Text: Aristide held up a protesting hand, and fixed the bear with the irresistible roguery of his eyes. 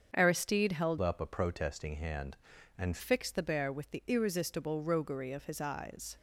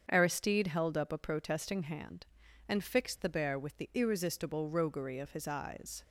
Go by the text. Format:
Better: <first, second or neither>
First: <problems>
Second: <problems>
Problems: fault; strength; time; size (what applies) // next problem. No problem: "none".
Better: second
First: starts louder than the rest; strong; until 1.1 s; 7 dB // changes voice from "up" to "and"; from 0.9 to 2.9 s; 2.0 s long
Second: starts louder than the rest; strong; until 1.1 s; 7.5 dB